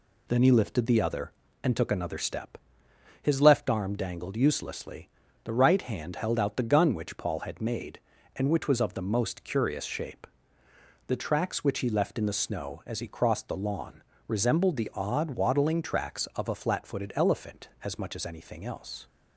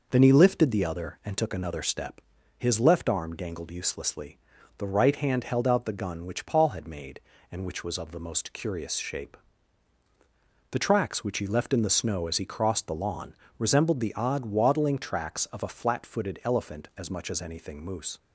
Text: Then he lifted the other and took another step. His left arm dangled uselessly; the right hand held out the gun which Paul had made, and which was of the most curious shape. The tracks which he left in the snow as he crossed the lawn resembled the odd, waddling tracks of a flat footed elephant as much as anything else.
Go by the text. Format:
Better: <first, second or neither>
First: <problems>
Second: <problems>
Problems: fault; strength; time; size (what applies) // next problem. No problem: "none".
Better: first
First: pauses between "lawn" and "resembled"; slight; at 14.0 s; 0.24 s long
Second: pauses between "lawn" and "resembled"; slight; at 13.3 s; 0.24 s long // says "moose" for "else"; at 17.8 s